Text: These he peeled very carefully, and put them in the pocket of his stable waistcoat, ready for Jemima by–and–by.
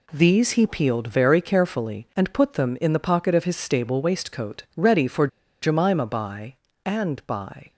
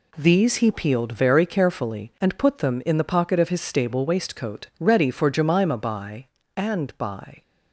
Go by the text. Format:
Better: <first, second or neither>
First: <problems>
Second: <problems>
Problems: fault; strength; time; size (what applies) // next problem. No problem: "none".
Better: second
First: pauses between "for" and "Jemima"; slight; at 5.2 s; 0.35 s long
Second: none